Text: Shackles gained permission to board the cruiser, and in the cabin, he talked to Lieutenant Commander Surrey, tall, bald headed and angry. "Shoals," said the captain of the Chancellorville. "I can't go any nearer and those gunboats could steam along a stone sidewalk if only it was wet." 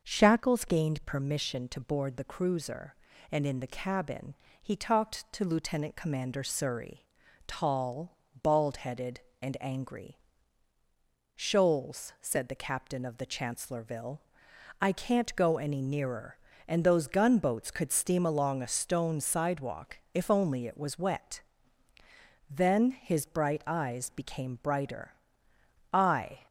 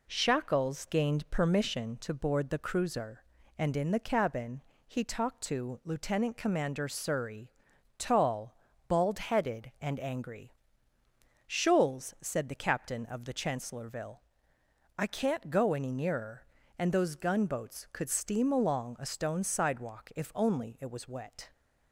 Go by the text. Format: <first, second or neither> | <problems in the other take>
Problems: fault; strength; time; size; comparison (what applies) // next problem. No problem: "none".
second | starts louder than the rest; noticeable; until 1.0 s; 6 dB // pauses between "sidewalk" and "if"; slight; at 19.9 s; 0.16 s long // goes on to say "Then his bright eyes became brighter I"; strong; from 22.4 s on; 3.9 s long